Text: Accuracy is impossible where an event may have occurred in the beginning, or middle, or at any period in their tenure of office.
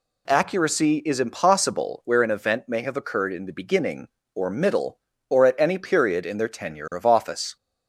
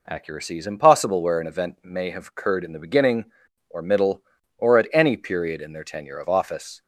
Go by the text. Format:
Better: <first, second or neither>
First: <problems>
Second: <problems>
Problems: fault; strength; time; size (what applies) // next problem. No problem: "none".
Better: neither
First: none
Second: none